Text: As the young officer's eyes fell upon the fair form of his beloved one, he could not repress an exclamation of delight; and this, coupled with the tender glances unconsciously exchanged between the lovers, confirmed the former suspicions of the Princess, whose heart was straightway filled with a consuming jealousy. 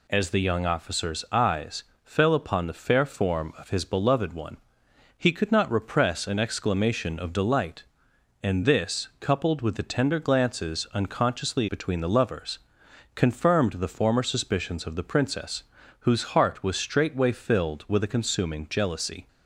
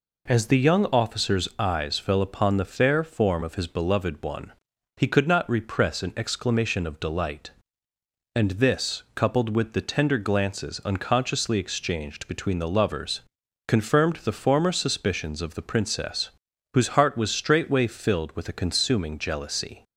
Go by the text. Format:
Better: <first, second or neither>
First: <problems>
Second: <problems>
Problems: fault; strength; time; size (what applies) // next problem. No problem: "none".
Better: second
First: pauses between "eyes" and "fell"; slight; at 1.8 s; 0.20 s long // skips "exchanged"; at 11.6 s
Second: none